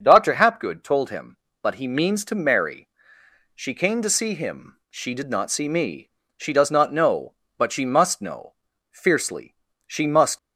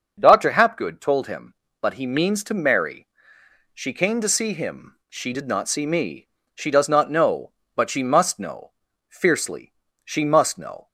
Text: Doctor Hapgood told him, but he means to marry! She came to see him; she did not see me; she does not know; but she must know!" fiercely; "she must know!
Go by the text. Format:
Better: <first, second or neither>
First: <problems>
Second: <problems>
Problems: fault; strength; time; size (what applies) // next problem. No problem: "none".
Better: second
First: starts louder than the rest; until 1.0 s; 6 dB // stops before "know"; at 10.3 s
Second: starts louder than the rest; until 1.1 s; 6 dB